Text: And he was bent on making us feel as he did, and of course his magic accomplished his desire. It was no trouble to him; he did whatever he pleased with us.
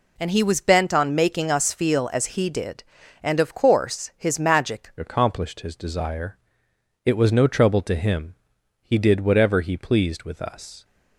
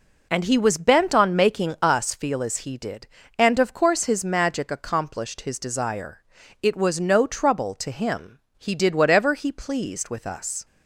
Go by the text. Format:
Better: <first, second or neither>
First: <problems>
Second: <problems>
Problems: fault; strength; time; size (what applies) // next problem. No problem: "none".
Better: second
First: changes voice at "accomplished"; from 4.9 s on; 5.9 s long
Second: none